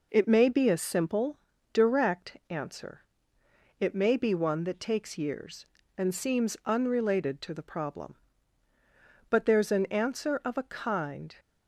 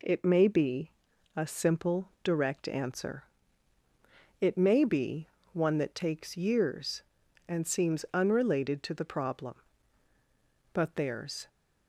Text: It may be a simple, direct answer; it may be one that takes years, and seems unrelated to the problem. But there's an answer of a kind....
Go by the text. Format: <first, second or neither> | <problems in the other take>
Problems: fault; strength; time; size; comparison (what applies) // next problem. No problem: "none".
first | pauses between "be" and "a"; noticeable; at 0.8 s; 0.46 s long // pauses between "be" and "one"; slight; at 5.2 s; 0.24 s long // stops before "an answer of a kind"; at 11.4 s